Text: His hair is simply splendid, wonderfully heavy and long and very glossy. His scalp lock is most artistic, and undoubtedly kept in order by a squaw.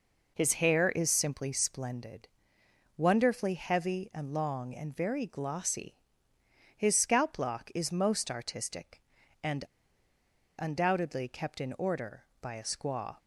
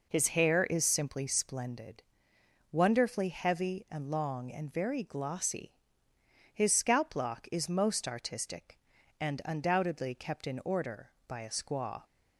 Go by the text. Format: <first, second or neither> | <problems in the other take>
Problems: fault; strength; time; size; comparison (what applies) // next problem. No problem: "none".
second | pauses between "and" and "undoubtedly"; noticeable; at 9.6 s; 0.96 s long